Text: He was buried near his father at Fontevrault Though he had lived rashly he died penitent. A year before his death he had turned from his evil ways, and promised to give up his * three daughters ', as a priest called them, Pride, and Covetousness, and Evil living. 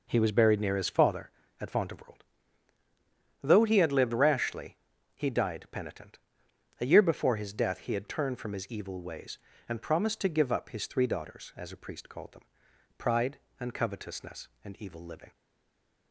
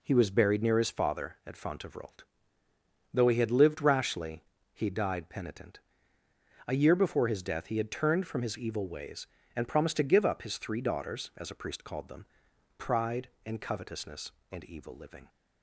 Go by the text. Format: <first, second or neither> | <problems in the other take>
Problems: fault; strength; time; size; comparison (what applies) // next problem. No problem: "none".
second | pauses between "Fontevrault" and "Though"; at 2.2 s; 1.2 s long; noticeable in the second // pauses between "rashly" and "he"; at 4.7 s; 0.40 s long; slight in the second // stays silent after the last word; slight; from 15.3 s on; 0.8 s long